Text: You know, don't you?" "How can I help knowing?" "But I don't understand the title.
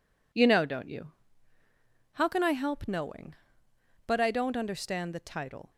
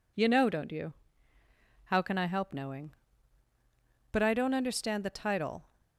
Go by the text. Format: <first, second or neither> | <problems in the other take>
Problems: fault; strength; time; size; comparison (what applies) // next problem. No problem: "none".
neither | none